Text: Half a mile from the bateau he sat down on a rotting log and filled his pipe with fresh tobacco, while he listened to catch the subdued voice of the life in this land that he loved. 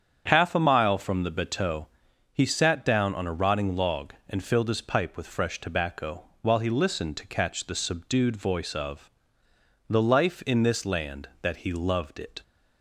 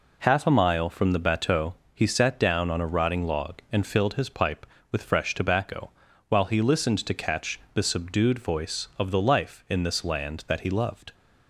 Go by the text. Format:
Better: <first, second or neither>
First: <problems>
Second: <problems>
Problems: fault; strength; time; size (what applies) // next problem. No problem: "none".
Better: second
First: starts louder than the rest; strong; until 1.2 s; 8 dB // pauses between "bateau" and "he"; noticeable; at 1.8 s; 0.46 s long // pauses between "of" and "the"; noticeable; at 9.0 s; 0.80 s long // goes on to say "It"; slight; from 12.1 s on; 0.24 s long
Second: pauses between "bateau" and "he"; slight; at 1.7 s; 0.22 s long